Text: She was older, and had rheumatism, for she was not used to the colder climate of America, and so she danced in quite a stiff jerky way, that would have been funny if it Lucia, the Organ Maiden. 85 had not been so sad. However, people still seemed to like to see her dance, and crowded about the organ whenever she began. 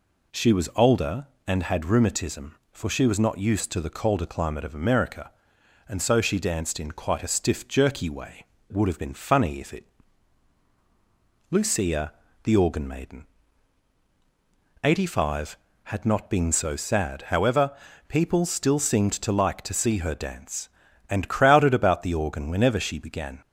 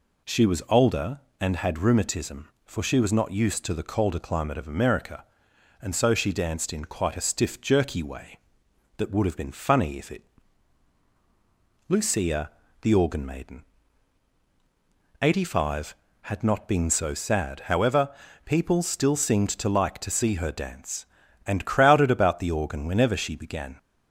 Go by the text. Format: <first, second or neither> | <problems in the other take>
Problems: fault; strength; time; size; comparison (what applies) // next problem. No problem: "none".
second | skips "that"; at 8.5 s // pauses between "it" and "Lucia"; strong; at 9.8 s; 1.6 s long; strong in the second